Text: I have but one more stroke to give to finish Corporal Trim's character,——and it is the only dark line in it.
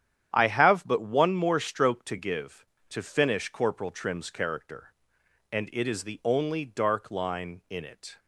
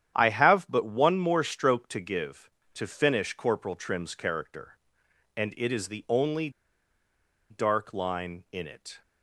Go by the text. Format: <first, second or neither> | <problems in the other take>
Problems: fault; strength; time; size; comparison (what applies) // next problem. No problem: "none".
first | starts louder than the rest; strong; until 1.1 s; 9.5 dB; strong in the first // pauses between "only" and "dark"; at 6.4 s; 1.0 s long